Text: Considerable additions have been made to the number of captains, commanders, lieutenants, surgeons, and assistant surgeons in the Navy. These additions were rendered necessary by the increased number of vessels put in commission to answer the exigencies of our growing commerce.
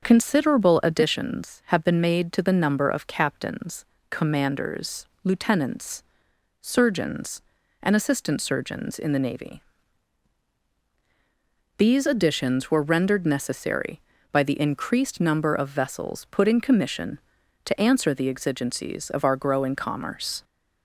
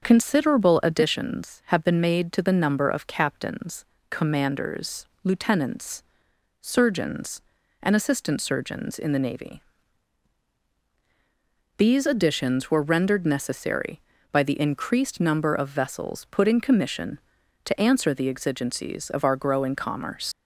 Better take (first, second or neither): first